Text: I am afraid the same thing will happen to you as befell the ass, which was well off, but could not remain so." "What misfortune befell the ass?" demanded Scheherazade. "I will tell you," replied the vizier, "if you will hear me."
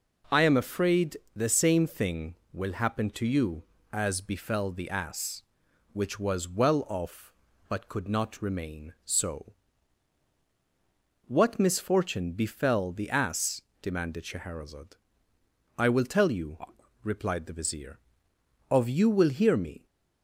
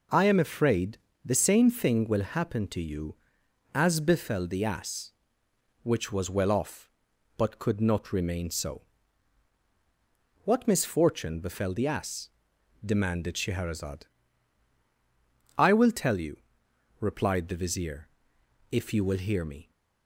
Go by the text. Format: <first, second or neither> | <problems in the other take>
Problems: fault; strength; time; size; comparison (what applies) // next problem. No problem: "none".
second | pauses between "afraid" and "the"; slight; at 1.1 s; 0.18 s long; slight in the second // says "of" for "if"; at 18.7 s